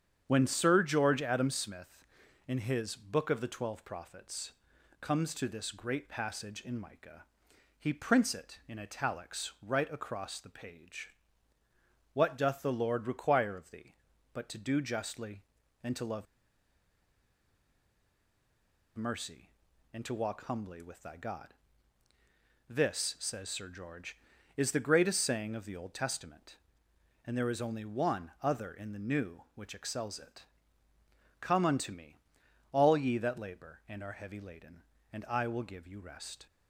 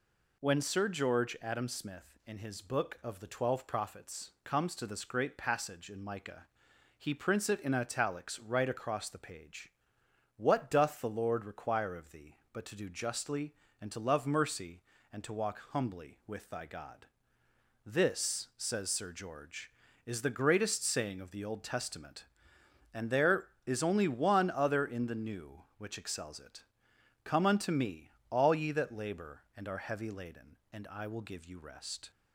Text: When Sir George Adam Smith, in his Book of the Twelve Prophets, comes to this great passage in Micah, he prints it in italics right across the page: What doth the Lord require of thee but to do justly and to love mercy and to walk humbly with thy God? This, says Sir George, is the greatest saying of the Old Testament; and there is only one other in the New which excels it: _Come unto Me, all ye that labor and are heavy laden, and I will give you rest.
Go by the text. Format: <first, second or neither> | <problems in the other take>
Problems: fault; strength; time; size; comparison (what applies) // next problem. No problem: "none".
second | starts louder than the rest; strong; until 1.2 s; 8 dB // pauses between "love" and "mercy"; strong; at 16.2 s; 2.7 s long